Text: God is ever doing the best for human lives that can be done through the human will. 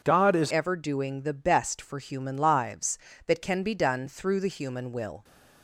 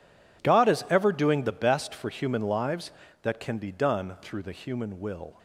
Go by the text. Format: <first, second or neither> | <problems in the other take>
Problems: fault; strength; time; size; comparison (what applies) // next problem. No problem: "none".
second | changes voice at "ever"; from 0.5 s on; 4.7 s long